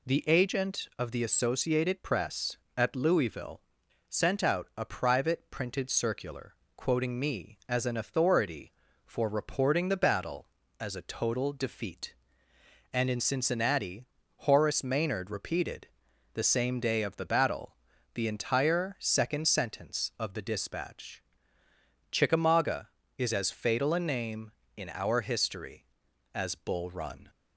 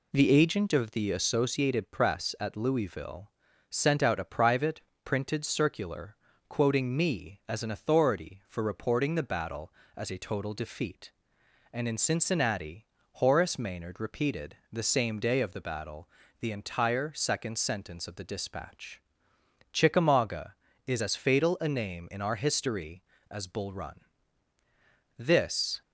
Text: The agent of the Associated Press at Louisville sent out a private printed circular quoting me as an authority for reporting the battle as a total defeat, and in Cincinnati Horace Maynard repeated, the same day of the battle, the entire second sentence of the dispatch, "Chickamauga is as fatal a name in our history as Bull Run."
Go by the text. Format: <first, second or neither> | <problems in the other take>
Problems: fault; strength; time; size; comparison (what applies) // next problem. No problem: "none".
first | pauses between "Louisville" and "sent"; at 3.3 s; 0.38 s long; noticeable in the first // pauses between "private" and "printed"; slight; at 4.8 s; 0.24 s long // pauses between "circular" and "quoting"; slight; at 6.1 s; 0.32 s long; slight in the first // pauses between "Cincinnati" and "Horace"; slight; at 12.8 s; 0.26 s long; slight in the first // goes on to say "This"; noticeable; from 25.1 s on; 0.62 s long